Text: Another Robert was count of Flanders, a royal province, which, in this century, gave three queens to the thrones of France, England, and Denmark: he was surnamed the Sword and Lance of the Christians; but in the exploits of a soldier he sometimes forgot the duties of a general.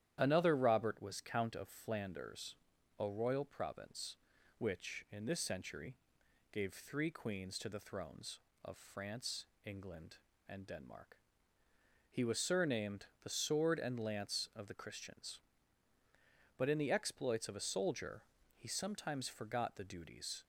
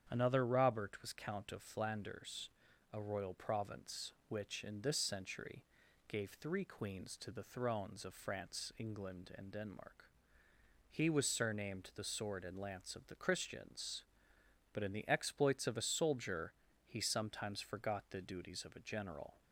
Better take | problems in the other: second | starts louder than the rest; strong; until 1.2 s; 11 dB; strong in the second // pauses between "surnamed" and "the"; slight; at 13.0 s; 0.16 s long // pauses between "soldier" and "he"; slight; at 18.2 s; 0.34 s long; slight in the second // stops before "of a general"; at 20.4 s

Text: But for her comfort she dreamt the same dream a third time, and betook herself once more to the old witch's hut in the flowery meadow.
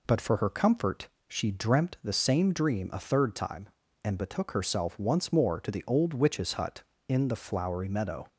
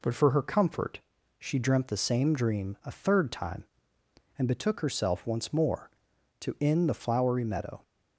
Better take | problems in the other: first | pauses between "comfort" and "she"; at 0.9 s; 0.40 s long; slight in the first // skips "the old witch's hut"; at 6.5 s

